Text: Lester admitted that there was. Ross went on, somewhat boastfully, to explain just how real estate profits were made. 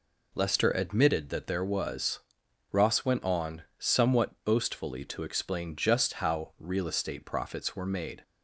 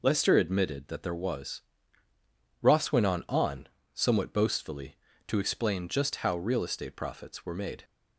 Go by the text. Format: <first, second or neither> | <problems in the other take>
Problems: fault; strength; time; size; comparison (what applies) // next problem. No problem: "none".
first | says "on" twice; at 3.2 s